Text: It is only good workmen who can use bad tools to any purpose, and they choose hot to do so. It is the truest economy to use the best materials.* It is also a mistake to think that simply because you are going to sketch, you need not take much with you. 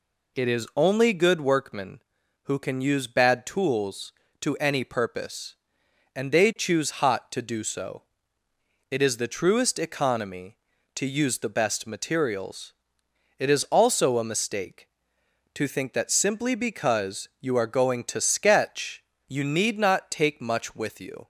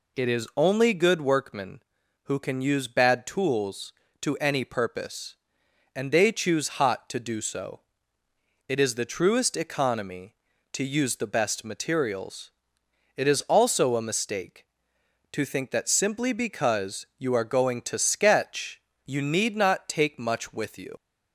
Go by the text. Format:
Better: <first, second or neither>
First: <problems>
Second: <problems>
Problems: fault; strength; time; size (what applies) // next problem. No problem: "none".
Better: first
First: none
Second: leaves "you" unfinished; at 20.9 s; 85 ms